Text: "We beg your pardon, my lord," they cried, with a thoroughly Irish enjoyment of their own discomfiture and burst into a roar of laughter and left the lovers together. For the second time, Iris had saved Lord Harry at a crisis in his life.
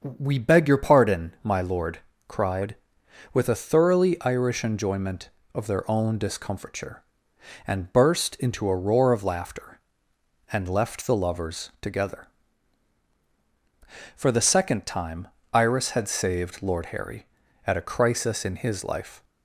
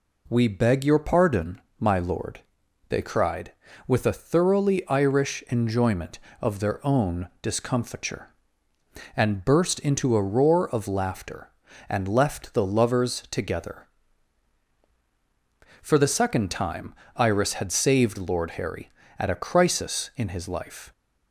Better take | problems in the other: second | starts louder than the rest; until 1.2 s; 7 dB // skips "they"; at 2.1 s

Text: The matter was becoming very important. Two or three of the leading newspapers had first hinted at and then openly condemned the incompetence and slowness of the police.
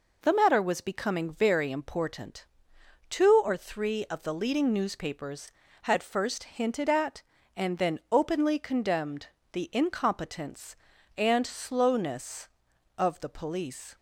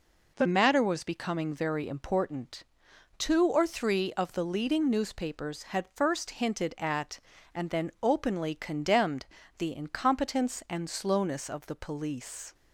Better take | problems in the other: neither | pauses between "condemned" and "the"; slight; the same in both

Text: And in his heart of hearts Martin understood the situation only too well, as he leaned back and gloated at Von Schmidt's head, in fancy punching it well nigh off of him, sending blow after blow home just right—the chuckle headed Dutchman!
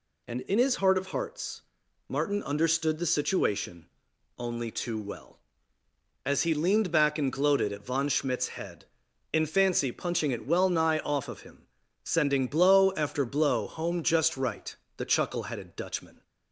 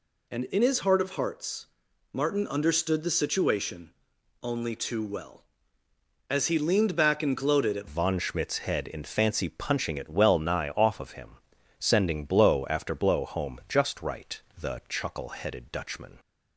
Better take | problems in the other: first | pauses between "hearts" and "Martin"; noticeable; at 1.6 s; 0.46 s long; noticeable in the first // pauses between "situation" and "only"; noticeable; at 3.9 s; 0.52 s long; noticeable in the first // changes voice at "Von"; from 7.8 s on; 8.3 s long

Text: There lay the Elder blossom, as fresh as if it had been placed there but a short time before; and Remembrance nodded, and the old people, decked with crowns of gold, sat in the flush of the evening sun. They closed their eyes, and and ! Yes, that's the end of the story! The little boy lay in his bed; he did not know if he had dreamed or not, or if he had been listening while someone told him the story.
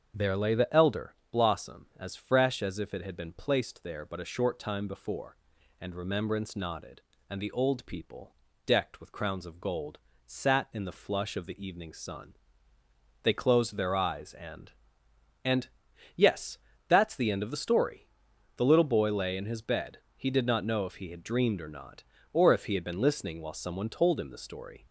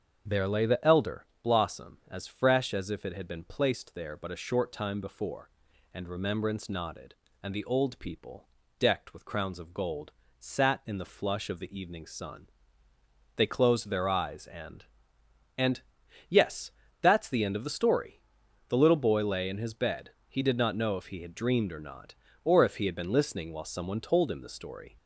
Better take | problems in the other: neither | starts louder than the rest; the same in both // pauses between "Elder" and "blossom"; slight; the same in both

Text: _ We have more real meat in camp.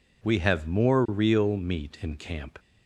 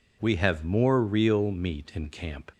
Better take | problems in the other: neither | none

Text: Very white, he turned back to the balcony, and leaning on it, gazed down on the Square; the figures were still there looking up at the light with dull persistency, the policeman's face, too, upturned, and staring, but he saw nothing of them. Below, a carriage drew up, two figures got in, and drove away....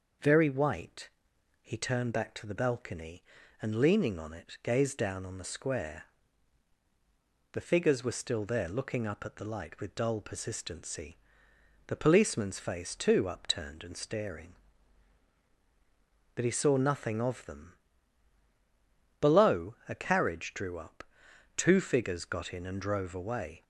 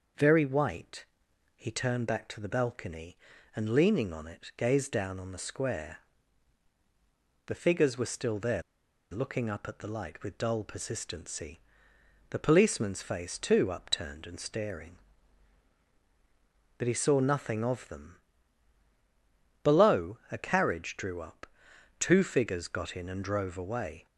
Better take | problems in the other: first | pauses between "there" and "looking"; noticeable; at 8.6 s; 0.49 s long

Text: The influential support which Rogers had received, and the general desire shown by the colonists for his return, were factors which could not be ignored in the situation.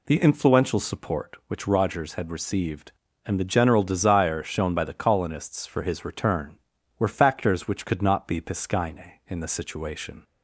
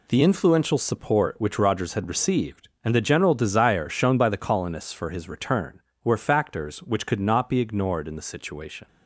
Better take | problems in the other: second | says "piscine" for "ignored"; at 8.3 s

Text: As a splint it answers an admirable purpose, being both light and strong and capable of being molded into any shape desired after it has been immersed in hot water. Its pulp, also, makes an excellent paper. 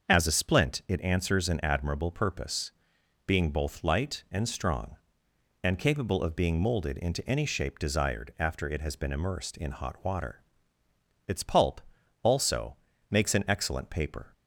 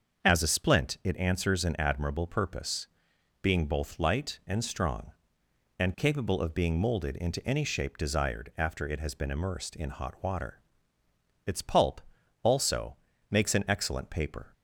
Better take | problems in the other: neither | starts louder than the rest; the same in both

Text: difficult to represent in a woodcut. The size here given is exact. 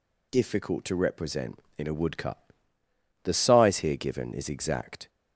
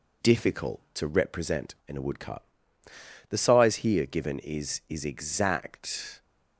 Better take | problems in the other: first | says "is" twice; at 4.8 s

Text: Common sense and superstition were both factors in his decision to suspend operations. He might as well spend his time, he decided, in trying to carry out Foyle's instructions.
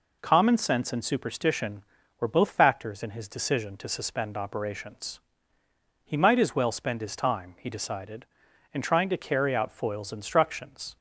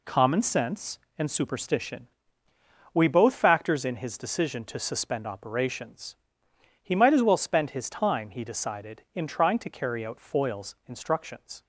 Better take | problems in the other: first | says "we" for "were"; at 2.9 s

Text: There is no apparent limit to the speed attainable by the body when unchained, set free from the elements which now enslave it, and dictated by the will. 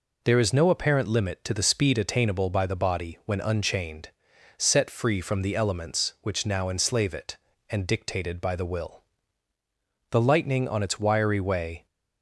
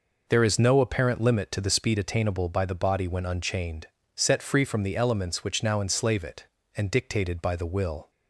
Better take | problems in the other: second | goes on to say "The lightning on its wiry way"; strong; from 10.1 s on; 1.7 s long

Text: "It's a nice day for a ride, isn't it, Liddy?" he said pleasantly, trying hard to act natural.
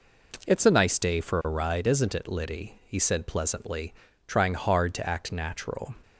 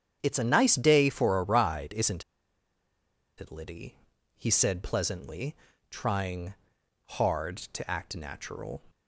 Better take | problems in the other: first | starts louder than the rest; strong; until 1.2 s; 8.5 dB // pauses between "isn't" and "it"; at 2.2 s; 1.1 s long // pauses between "trying" and "hard"; noticeable; at 6.5 s; 0.52 s long

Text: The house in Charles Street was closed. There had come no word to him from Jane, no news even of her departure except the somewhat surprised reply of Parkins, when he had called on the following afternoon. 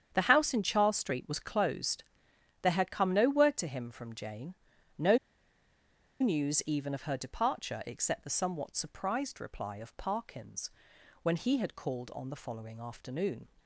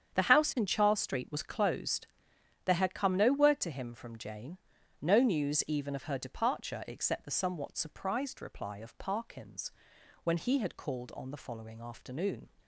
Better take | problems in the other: second | starts louder than the rest; strong; until 1.1 s; 8.5 dB; strong in the second // pauses between "no" and "news"; at 5.1 s; 1.0 s long

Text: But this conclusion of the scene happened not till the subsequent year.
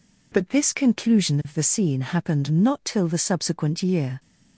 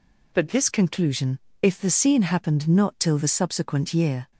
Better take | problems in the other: first | says "if" for "of"; at 1.6 s

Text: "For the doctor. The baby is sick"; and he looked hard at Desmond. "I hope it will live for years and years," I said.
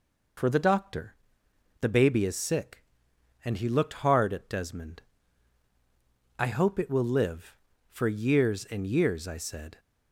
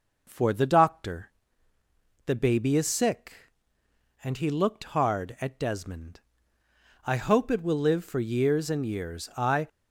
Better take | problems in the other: first | stops before "said"; at 9.6 s

